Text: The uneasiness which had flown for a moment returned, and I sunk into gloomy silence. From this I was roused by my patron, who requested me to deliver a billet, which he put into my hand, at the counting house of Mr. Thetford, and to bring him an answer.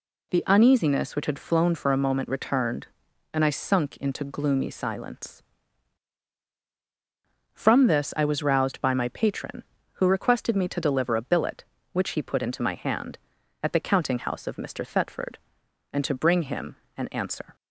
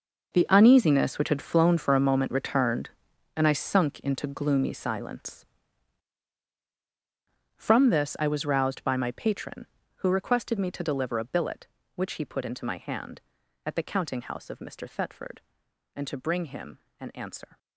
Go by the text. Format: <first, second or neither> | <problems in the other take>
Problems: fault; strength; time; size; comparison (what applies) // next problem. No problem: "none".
first | gets quieter; strong; throughout; 14 dB // pauses between "him" and "an"; slight; at 16.7 s; 0.20 s long; slight in the first